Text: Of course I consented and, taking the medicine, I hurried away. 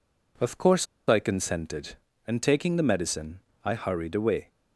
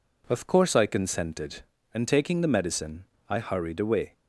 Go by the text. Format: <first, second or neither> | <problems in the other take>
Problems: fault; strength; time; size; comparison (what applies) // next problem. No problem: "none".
second | pauses between "course" and "I"; slight; at 0.8 s; 0.22 s long